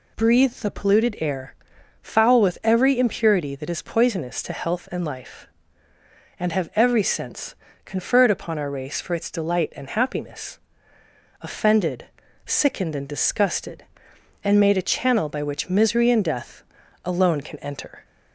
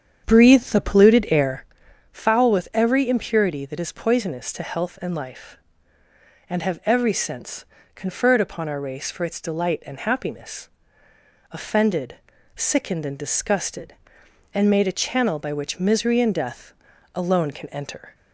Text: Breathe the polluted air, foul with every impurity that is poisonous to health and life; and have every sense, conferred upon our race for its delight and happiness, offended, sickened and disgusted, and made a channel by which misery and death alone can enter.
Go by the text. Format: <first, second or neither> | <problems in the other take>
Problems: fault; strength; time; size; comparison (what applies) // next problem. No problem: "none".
first | starts louder than the rest; strong; until 1.7 s; 8 dB // pauses between "death" and "alone"; at 16.7 s; 0.42 s long; also in the first